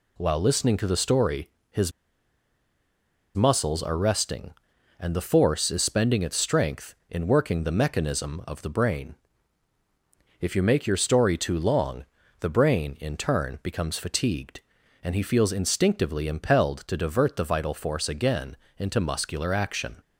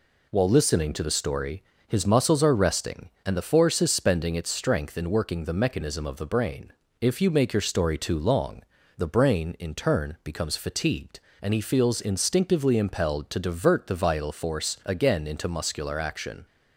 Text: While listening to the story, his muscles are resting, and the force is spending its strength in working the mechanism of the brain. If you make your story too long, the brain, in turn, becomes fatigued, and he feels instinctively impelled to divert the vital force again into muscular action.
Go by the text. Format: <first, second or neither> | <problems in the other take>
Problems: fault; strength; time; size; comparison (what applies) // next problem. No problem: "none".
second | pauses between "his" and "muscles"; strong; at 1.9 s; 1.4 s long // pauses between "again" and "into"; slight; at 18.5 s; 0.22 s long